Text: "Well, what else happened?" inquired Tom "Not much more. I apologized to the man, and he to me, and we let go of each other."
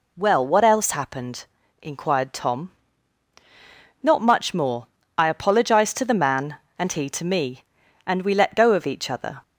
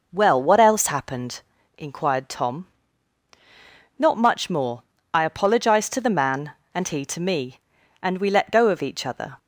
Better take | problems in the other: first | starts louder than the rest; noticeable; until 1.9 s; 5 dB // pauses between "Tom" and "Not"; strong; at 2.6 s; 1.3 s long; strong in the first

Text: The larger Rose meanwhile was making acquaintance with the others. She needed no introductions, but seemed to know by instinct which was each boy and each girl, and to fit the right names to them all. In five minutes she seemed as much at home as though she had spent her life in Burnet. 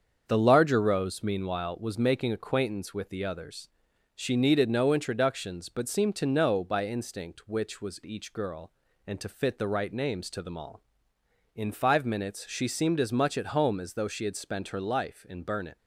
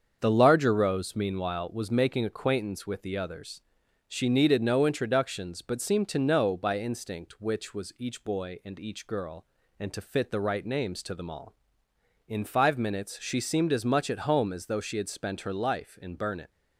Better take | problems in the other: second | starts louder than the rest; until 1.2 s; 7 dB; also in the second // skips "each boy and"; at 8.0 s

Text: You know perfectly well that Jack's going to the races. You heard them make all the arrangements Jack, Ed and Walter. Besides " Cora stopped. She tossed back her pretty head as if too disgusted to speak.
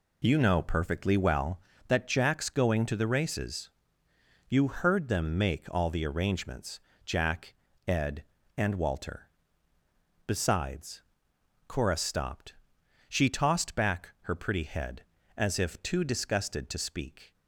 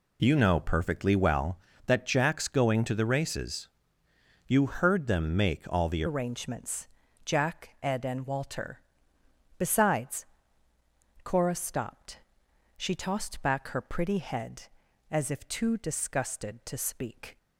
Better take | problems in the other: first | changes voice at "arrangements"; from 6.0 s on; 11.3 s long // pauses between "arrangements" and "Jack"; slight; at 6.8 s; 0.36 s long; slight in the first

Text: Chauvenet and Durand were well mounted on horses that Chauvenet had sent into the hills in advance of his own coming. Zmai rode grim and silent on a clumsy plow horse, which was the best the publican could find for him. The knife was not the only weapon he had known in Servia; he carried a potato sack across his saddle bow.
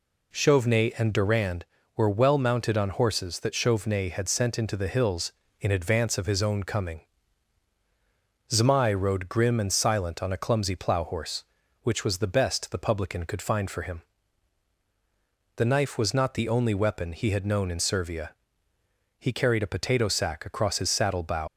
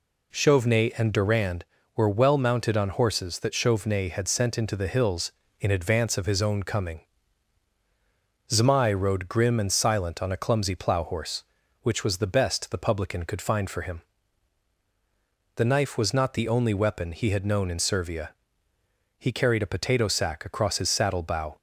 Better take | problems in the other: second | leaves "bow" unfinished; at 21.4 s; 100 ms

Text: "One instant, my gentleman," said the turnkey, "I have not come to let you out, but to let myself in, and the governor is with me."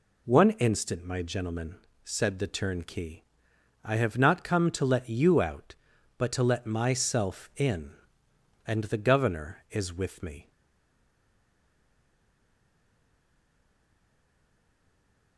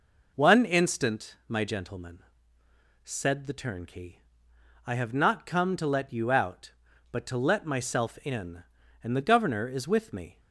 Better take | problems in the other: second | stays silent after the last word; strong; from 10.5 s on; 4.8 s long

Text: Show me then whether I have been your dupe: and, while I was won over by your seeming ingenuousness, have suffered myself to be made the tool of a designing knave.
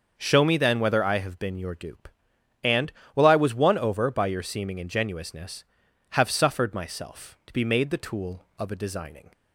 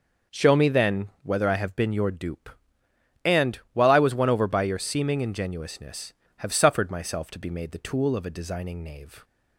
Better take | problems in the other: second | starts louder than the rest; until 1.1 s; 6.5 dB // stops before "knave"; at 9.3 s

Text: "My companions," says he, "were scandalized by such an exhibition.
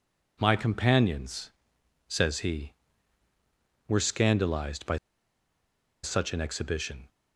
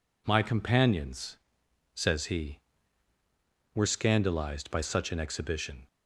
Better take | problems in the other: second | pauses between "by" and "such"; at 4.9 s; 1.0 s long

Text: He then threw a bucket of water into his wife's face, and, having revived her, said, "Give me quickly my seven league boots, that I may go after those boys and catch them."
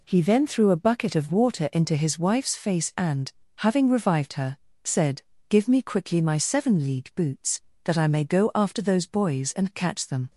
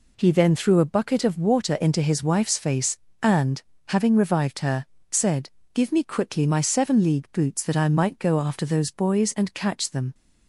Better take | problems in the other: first | says "might" for "may"; at 7.8 s

